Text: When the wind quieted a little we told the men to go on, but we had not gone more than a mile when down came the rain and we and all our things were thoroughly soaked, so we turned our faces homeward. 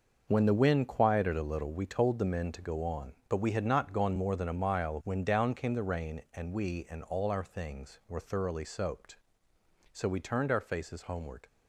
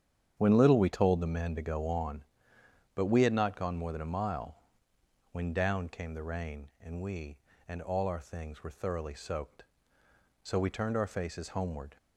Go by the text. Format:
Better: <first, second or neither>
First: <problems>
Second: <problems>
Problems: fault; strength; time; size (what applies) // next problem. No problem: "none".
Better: first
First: starts louder than the rest; noticeable; until 1.3 s; 6 dB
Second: starts louder than the rest; strong; until 1.4 s; 8.5 dB // skips "the wind quieted a"; at 0.5 s // pauses between "mile" and "when"; noticeable; at 4.5 s; 0.74 s long